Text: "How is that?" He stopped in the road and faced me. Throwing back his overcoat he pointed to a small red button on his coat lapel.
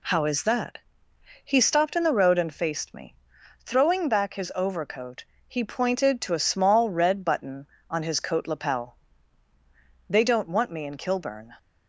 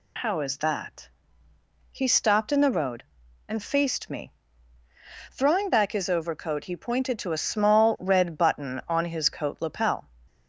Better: second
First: pauses between "overcoat" and "he"; slight; at 5.2 s; 0.22 s long // goes on to say "They don't want me in Kilburn"; from 10.0 s on; 1.4 s long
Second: none

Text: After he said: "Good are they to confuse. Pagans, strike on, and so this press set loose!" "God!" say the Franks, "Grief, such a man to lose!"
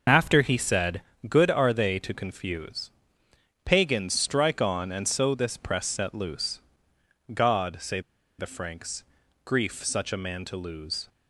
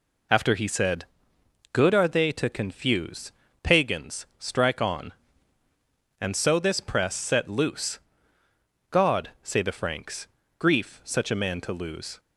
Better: second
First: pauses between "say" and "the"; at 8.0 s; 0.38 s long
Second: none

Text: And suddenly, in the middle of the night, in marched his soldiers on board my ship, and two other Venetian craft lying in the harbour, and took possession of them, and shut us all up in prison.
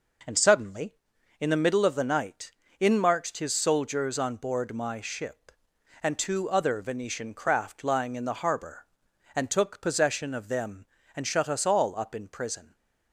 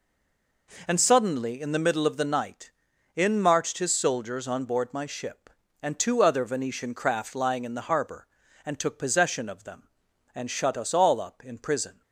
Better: first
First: none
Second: stays silent before the first word; slight; until 0.6 s; 0.6 s long

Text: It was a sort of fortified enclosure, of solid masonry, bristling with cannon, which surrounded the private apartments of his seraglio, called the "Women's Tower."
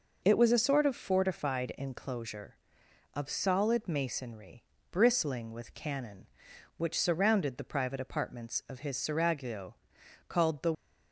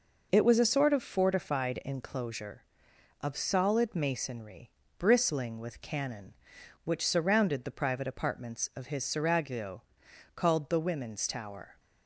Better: second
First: stops before "Women's Tower"; at 10.7 s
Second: none

